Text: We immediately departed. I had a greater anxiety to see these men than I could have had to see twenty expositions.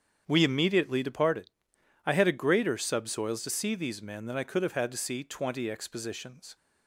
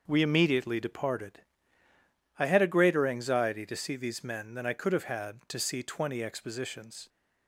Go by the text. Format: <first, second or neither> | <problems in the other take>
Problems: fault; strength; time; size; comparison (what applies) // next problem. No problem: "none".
second | starts louder than the rest; strong; until 1.2 s; 8 dB; noticeable in the second // says "subsoils" for "anxiety"; at 2.7 s